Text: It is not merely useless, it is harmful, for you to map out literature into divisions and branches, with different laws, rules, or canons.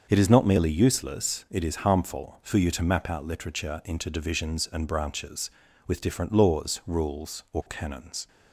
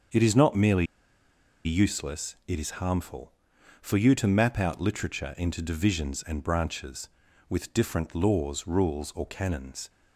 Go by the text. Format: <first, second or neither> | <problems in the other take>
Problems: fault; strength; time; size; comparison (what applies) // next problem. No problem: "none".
first | starts louder than the rest; until 1.9 s; 7 dB; also in the first // pauses between "merely" and "useless"; noticeable; at 0.8 s; 0.78 s long